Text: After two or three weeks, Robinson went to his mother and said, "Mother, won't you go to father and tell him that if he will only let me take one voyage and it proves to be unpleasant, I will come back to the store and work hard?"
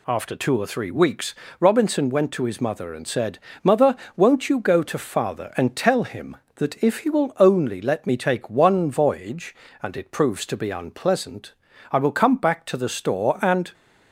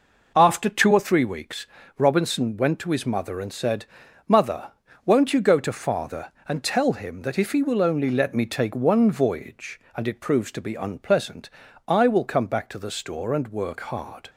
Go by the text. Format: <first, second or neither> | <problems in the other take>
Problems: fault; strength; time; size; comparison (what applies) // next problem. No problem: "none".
second | stops before "work hard"; at 13.7 s